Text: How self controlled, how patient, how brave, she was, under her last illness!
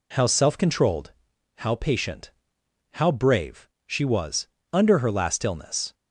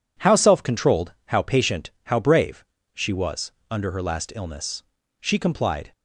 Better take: first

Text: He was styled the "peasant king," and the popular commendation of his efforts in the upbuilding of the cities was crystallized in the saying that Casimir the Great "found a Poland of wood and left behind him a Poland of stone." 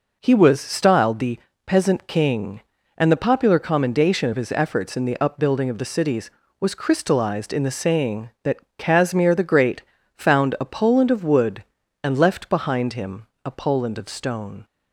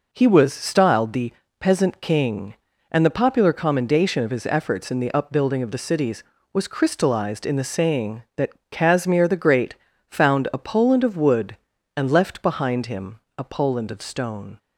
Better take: neither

